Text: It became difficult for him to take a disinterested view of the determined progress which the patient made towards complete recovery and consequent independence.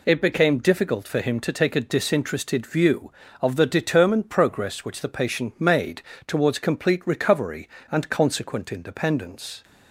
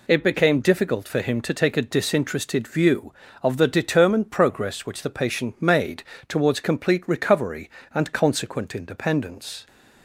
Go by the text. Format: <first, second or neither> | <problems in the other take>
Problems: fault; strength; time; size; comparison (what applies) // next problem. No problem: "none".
neither | pauses between "made" and "towards"; slight; the same in both